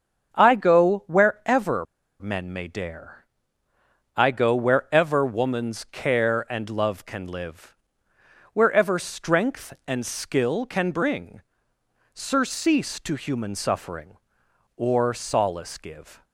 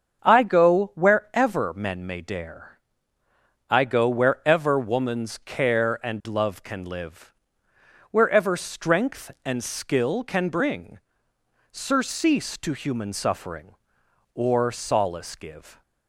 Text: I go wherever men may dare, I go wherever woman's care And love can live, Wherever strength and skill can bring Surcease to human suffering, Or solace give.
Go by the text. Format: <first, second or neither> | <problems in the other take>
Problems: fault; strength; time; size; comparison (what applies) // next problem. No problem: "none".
second | starts louder than the rest; until 1.3 s; 7 dB; also in the second // pauses between "wherever" and "men"; slight; at 1.8 s; 0.34 s long // pauses between "bring" and "Surcease"; noticeable; at 11.4 s; 0.72 s long; noticeable in the second